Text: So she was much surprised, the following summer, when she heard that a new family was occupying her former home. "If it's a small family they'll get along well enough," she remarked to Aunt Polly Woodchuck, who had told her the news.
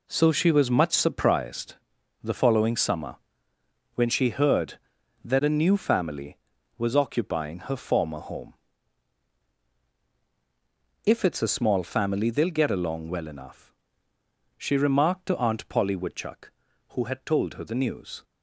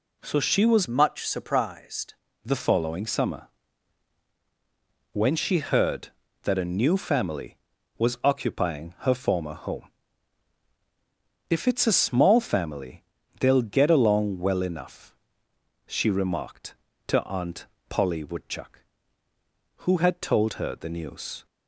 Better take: first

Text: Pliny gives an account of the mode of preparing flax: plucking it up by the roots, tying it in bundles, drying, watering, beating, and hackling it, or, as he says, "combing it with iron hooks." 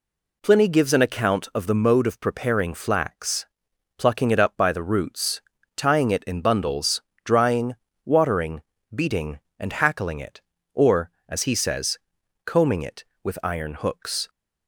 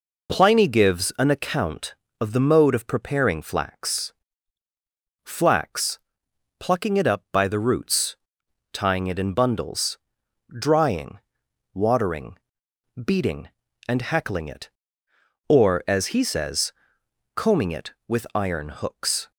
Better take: first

